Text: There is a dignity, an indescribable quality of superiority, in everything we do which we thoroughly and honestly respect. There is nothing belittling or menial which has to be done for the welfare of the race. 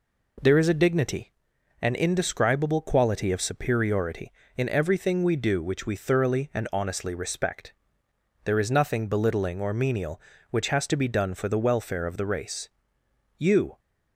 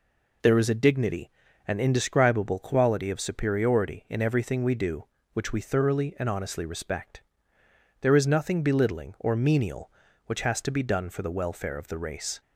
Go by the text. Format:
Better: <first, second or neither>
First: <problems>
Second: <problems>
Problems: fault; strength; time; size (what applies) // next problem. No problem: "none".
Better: second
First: goes on to say "You"; slight; from 13.3 s on; 0.42 s long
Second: none